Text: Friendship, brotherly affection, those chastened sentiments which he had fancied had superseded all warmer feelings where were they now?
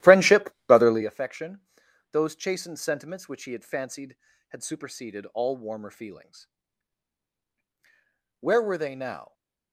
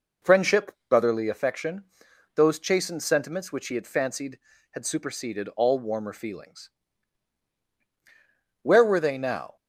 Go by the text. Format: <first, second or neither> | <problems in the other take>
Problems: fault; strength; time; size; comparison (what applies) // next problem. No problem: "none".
second | starts louder than the rest; strong; until 1.1 s; 13.5 dB // pauses between "feelings" and "where"; strong; at 6.4 s; 1.9 s long; strong in the second